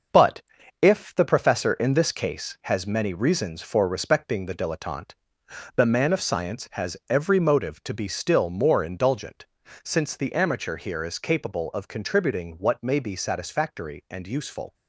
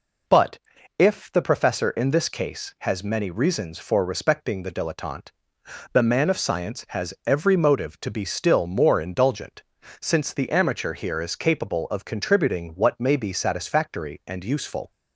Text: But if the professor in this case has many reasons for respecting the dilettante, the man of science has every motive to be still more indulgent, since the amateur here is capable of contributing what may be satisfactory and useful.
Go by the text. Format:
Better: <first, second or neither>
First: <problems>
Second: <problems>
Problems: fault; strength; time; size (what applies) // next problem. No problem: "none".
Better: second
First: gets quieter; throughout; 6.5 dB // pauses between "But" and "if"; at 0.4 s; 0.40 s long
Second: pauses between "But" and "if"; at 0.5 s; 0.40 s long